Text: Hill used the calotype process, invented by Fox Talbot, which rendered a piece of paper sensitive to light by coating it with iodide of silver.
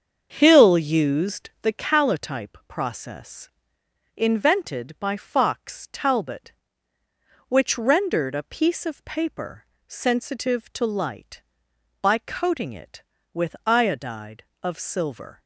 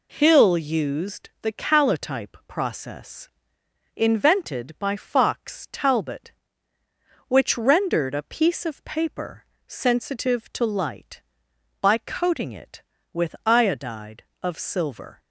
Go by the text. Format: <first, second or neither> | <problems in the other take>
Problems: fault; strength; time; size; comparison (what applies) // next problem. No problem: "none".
second | starts louder than the rest; until 1.9 s; 7 dB // pauses between "paper" and "sensitive"; slight; at 9.6 s; 0.24 s long; slight in the second